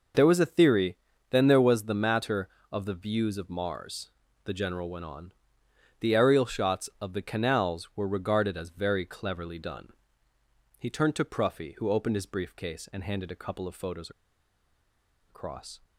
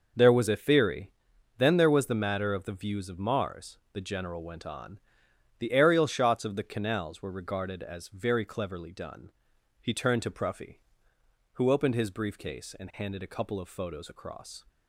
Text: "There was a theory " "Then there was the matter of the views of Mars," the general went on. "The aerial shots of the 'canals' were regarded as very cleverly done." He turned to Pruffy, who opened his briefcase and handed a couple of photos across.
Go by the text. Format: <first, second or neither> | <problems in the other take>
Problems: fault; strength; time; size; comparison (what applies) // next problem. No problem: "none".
second | pauses between "photos" and "across"; at 14.0 s; 1.1 s long